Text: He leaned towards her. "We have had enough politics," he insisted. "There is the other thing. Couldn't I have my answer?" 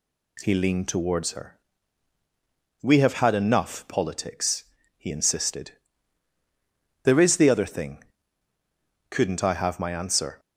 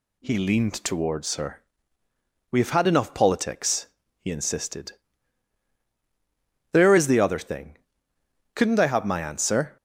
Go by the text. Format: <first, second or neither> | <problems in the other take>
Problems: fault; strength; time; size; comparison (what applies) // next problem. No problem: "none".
neither | none